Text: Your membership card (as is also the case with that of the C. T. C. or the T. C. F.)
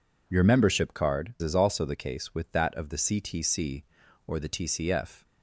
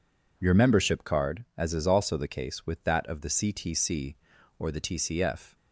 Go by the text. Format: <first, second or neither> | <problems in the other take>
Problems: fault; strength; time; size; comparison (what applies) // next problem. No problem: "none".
second | skips "as"; at 1.3 s